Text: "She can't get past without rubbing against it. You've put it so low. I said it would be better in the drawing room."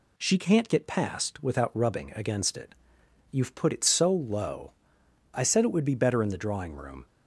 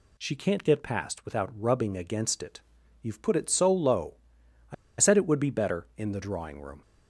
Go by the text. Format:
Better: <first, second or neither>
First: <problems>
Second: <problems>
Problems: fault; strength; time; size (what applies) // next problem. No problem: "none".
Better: first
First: none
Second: pauses between "I" and "said"; slight; at 4.7 s; 0.24 s long